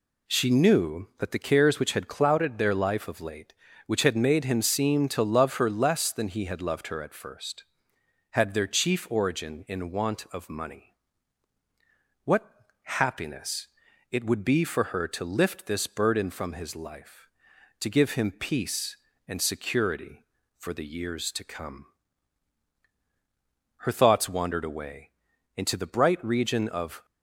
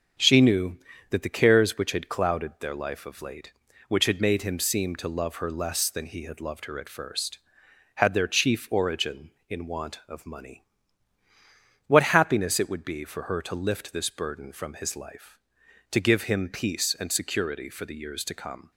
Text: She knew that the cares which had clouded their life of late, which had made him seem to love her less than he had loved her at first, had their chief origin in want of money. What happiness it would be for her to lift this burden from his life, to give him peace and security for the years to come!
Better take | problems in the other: second | pauses between "What" and "happiness"; slight; at 12.4 s; 0.34 s long // pauses between "happiness" and "it"; at 13.6 s; 0.44 s long // goes on to say "Her thoughts wandered away into the bright region of"; strong; from 23.7 s on; 3.2 s long

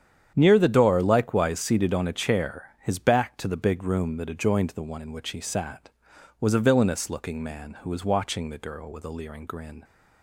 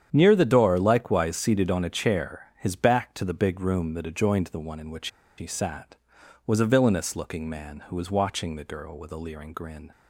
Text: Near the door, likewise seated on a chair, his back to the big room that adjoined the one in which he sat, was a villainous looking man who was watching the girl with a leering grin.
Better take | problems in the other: first | starts louder than the rest; strong; until 1.1 s; 9 dB; strong in the first // pauses between "which" and "he"; slight; at 5.0 s; 0.30 s long

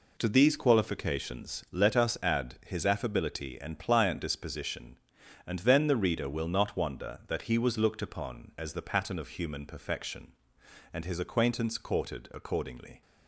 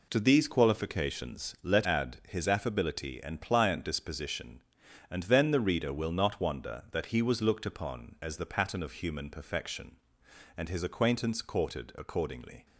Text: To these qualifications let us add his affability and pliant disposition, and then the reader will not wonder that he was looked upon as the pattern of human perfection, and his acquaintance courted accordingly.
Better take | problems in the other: first | skips "us"; at 1.8 s

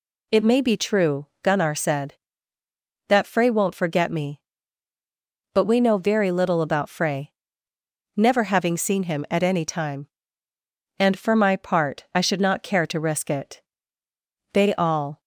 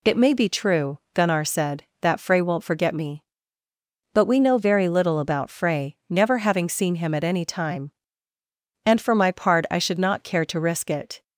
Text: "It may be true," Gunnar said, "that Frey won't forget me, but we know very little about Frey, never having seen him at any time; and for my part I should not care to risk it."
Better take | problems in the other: second | goes on to say "They all"; noticeable; from 14.5 s on; 0.68 s long

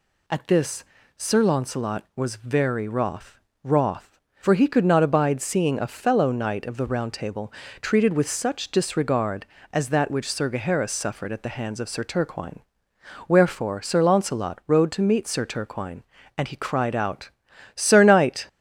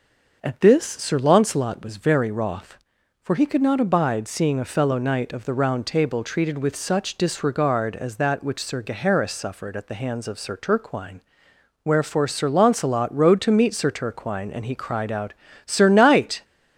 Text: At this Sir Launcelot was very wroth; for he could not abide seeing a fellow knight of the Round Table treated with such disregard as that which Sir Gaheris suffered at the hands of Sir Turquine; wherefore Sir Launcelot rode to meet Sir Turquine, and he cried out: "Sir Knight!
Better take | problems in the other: second | pauses between "this" and "Sir"; slight; at 0.8 s; 0.32 s long // says "wroth" twice; at 3.6 s // pauses between "Table" and "treated"; slight; at 7.5 s; 0.28 s long

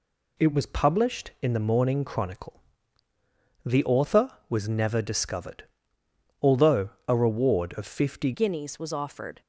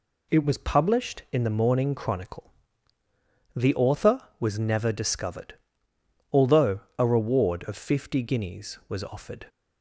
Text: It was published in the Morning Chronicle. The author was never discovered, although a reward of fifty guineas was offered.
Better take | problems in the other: second | pauses between "although" and "a"; slight; at 6.9 s; 0.16 s long; slight in the second // changes voice at "guineas"; from 8.3 s on; 1.1 s long

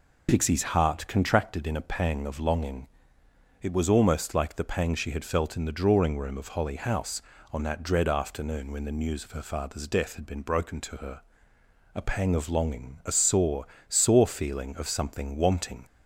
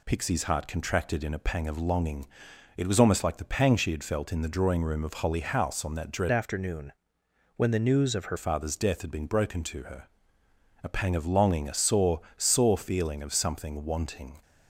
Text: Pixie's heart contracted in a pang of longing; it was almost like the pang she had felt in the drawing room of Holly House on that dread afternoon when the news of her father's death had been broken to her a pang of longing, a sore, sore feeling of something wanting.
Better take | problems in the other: first | changes voice from "afternoon" to "her"; from 6.3 to 8.3 s; 2.0 s long // pauses between "afternoon" and "when"; noticeable; at 6.9 s; 0.64 s long // pauses between "her" and "a"; noticeable; at 10.0 s; 0.76 s long; noticeable in the first

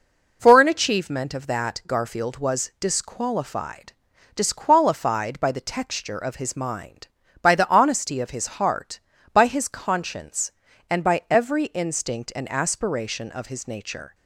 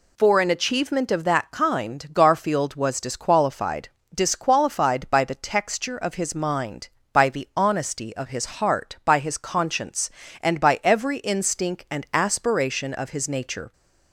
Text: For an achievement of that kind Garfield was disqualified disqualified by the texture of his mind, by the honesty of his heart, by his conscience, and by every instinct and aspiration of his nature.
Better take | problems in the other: second | skips "kind"; at 1.8 s // pauses between "disqualified" and "disqualified"; at 3.9 s; 0.42 s long; slight in the second

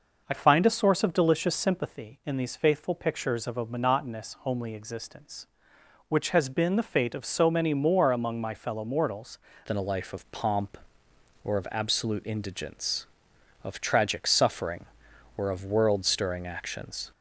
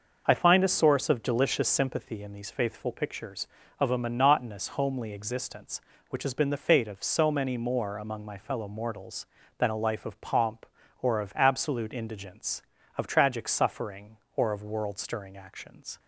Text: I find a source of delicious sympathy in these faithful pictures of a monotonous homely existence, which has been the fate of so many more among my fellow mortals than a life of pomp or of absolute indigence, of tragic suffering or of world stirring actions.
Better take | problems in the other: second | changes voice at "than"; from 9.6 s on; 7.5 s long

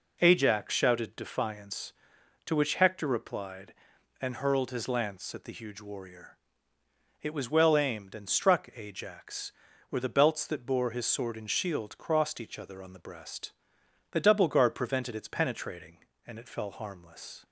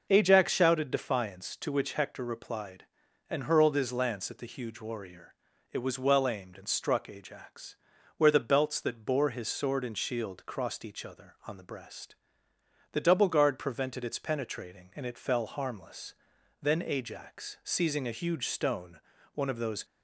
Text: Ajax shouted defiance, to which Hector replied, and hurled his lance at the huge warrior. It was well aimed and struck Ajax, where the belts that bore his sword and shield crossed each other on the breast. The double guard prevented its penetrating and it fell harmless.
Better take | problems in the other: first | goes on to say "Then Ajax seizing a huge stone one of those"; strong; from 16.6 s on; 3.2 s long

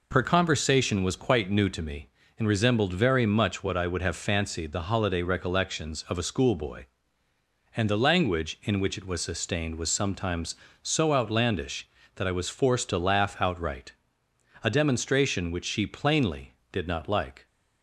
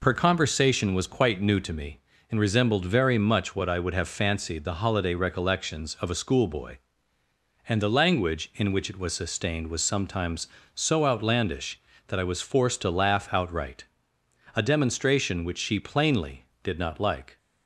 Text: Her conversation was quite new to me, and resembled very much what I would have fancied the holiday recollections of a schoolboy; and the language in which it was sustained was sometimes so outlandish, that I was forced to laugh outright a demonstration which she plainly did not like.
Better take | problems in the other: neither | pauses between "outright" and "a"; noticeable; the same in both

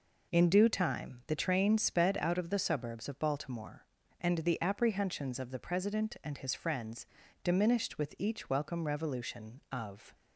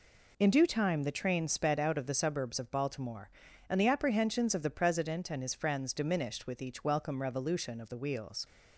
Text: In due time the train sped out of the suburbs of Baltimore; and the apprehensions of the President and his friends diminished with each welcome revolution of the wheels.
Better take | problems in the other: second | pauses between "friends" and "diminished"; at 7.0 s; 0.38 s long // stops before "the wheels"; at 10.1 s

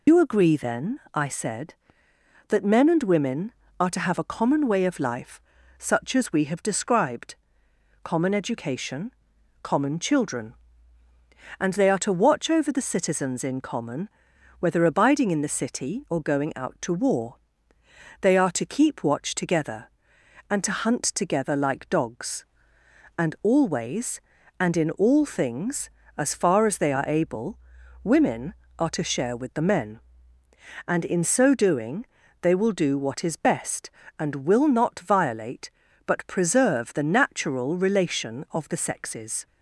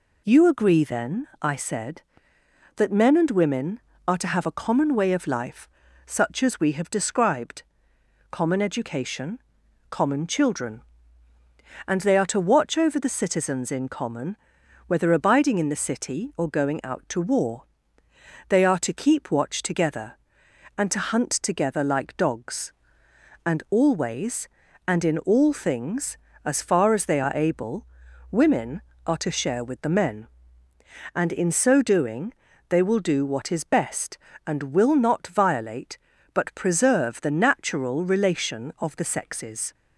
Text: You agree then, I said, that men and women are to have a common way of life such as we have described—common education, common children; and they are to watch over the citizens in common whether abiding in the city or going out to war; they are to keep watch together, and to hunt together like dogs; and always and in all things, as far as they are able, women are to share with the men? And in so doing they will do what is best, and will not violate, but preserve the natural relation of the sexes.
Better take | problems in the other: second | loses the start of "You"; at 0.0 s; 95 ms // pauses between "life" and "such"; slight; at 5.4 s; 0.36 s long; slight in the second // pauses between "common" and "whether"; noticeable; at 14.0 s; 0.52 s long; noticeable in the second // pauses between "doing" and "they"; slight; at 32.0 s; 0.36 s long; slight in the second

